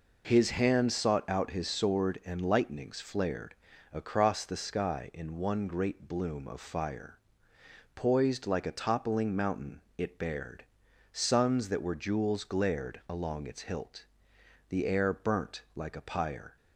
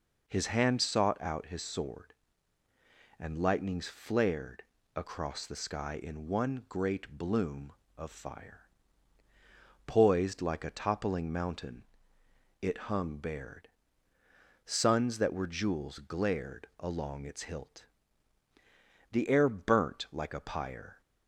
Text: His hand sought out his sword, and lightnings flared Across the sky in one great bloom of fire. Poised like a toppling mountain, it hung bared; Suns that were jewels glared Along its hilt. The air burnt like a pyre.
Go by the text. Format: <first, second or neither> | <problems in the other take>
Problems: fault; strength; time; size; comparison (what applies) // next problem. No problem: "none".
second | pauses between "flared" and "Across"; at 3.5 s; 0.38 s long; slight in the second // skips "hung"; at 10.1 s